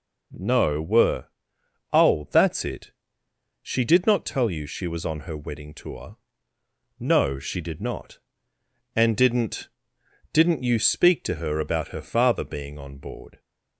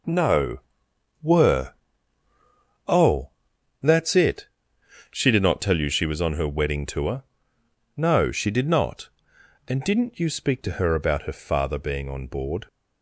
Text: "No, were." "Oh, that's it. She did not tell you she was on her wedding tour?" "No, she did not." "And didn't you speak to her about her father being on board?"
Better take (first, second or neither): second